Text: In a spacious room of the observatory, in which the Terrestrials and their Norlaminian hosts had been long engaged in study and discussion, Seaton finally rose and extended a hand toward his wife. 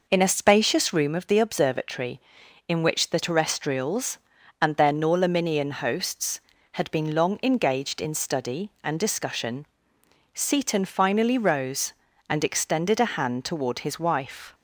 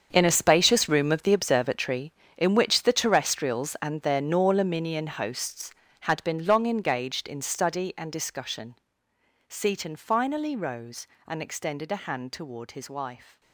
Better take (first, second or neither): first